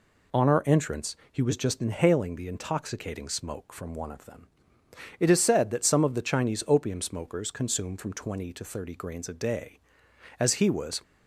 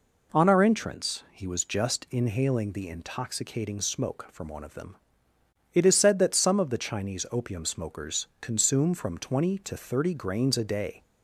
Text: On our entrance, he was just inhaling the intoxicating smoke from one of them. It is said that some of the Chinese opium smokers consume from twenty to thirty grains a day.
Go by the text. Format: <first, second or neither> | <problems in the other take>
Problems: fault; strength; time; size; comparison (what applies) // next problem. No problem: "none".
second | goes on to say "As he was"; noticeable; from 10.3 s on; 0.64 s long